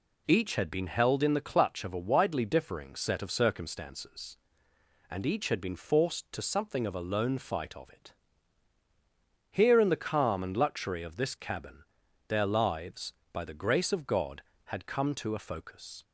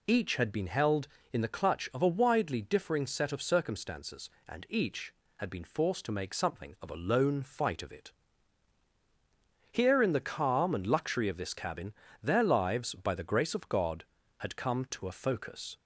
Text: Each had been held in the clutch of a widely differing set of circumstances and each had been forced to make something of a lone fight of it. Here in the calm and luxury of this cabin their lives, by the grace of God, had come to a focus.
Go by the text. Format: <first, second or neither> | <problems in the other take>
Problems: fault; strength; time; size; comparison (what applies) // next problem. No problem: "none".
second | skips "make"; at 6.4 s // pauses between "cabin" and "their"; at 11.8 s; 0.44 s long; slight in the second